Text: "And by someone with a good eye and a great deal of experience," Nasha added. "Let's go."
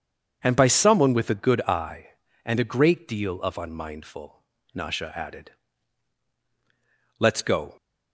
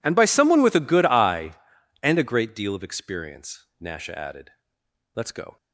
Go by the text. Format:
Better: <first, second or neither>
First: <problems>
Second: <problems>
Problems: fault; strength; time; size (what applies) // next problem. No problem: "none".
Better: second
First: says "unmindful" for "experience"; at 3.5 s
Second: none